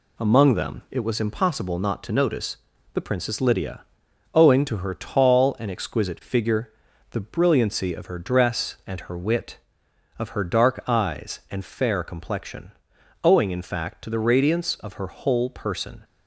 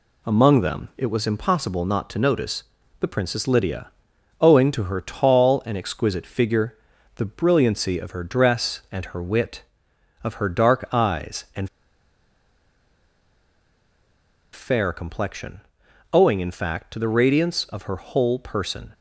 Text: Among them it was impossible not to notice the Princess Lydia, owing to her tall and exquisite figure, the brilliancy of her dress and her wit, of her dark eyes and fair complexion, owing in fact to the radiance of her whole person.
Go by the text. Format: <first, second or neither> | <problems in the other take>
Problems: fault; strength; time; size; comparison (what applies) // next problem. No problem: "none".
first | pauses between "notice" and "the"; slight; at 2.6 s; 0.36 s long; slight in the first // pauses between "and" and "fair"; strong; at 11.6 s; 2.8 s long